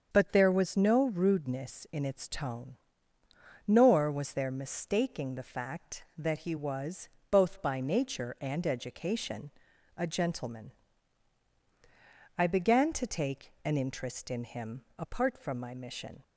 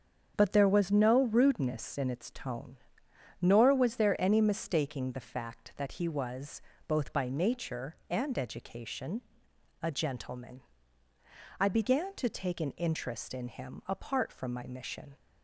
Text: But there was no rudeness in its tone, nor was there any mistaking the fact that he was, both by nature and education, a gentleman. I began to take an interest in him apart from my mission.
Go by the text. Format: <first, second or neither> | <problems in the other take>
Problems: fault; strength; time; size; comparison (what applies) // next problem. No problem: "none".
second | starts louder than the rest; strong; until 1.1 s; 7 dB; strong in the second // skips "any"; at 4.5 s